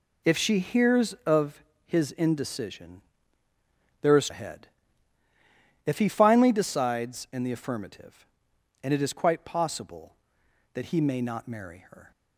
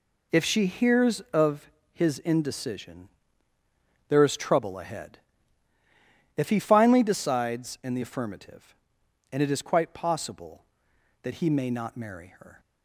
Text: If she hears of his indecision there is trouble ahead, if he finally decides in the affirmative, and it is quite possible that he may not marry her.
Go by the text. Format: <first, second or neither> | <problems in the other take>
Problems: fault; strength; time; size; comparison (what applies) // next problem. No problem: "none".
second | pauses between "of" and "his"; slight; at 1.6 s; 0.22 s long; slight in the second // pauses between "indecision" and "there"; at 3.0 s; 1.0 s long; also in the second // skips "trouble"; at 4.2 s